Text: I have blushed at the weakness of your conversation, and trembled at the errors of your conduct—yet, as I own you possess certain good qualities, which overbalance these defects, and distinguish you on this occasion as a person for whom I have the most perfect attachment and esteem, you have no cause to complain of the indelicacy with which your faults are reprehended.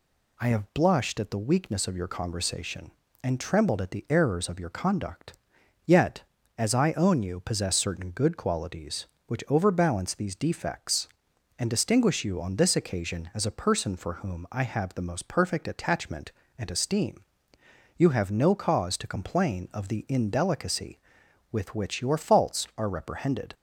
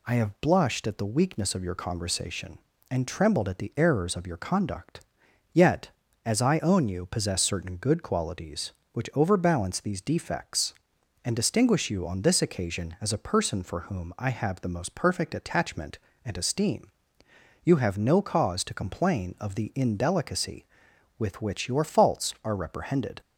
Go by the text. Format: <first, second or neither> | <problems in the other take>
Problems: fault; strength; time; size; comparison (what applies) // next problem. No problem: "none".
neither | none